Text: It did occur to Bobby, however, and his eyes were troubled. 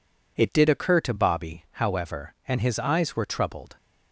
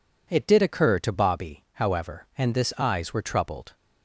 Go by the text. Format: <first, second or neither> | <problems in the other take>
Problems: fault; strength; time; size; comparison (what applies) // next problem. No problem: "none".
first | says "this" for "his"; at 2.5 s